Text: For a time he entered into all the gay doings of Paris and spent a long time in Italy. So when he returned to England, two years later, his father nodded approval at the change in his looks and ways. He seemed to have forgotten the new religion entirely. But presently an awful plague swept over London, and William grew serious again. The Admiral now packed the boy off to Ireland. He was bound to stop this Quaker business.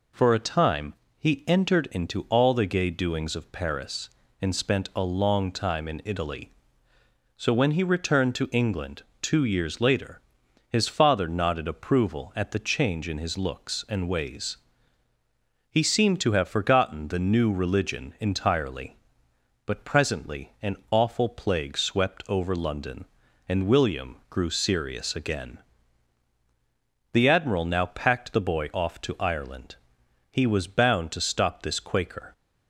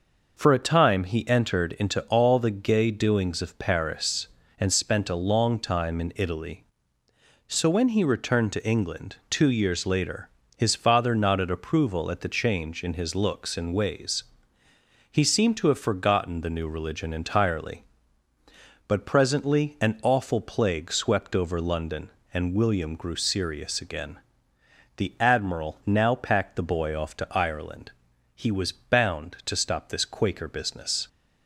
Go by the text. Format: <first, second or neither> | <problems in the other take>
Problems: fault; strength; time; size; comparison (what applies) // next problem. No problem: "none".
second | pauses between "time" and "he"; slight; at 0.9 s; 0.24 s long // pauses between "an" and "awful"; slight; at 20.7 s; 0.16 s long // stops before "business"; at 32.3 s